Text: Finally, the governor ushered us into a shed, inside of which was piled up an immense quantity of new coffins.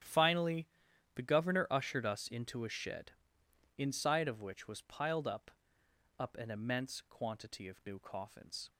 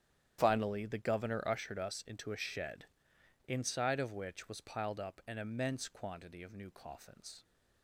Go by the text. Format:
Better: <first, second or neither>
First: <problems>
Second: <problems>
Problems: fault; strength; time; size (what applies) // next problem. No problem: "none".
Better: second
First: starts louder than the rest; strong; until 1.5 s; 10 dB // says "up" twice; at 6.1 s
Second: starts louder than the rest; strong; until 1.4 s; 10 dB